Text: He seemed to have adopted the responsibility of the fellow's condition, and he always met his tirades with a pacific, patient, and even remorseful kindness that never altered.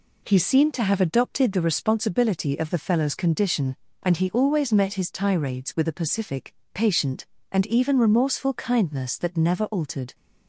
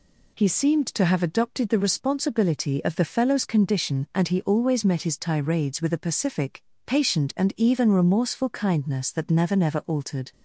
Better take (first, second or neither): first